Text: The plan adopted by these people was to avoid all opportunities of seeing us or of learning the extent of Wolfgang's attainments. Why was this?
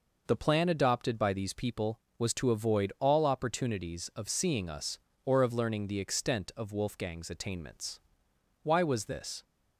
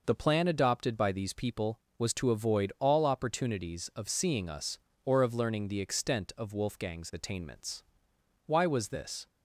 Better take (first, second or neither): neither